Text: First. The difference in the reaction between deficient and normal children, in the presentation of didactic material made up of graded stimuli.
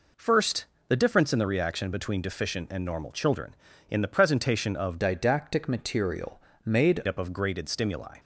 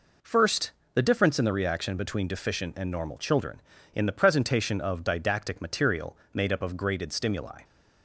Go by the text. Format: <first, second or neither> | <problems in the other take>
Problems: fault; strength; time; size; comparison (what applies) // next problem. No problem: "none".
second | changes voice from "didactic" to "made"; from 5.0 to 7.0 s; 2.0 s long // pauses between "material" and "made"; slight; at 6.3 s; 0.24 s long; slight in the second